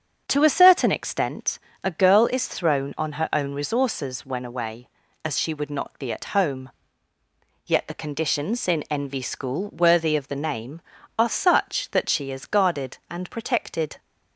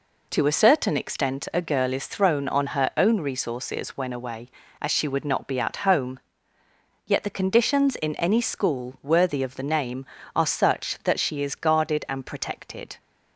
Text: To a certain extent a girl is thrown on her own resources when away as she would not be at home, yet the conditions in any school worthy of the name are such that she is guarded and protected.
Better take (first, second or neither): second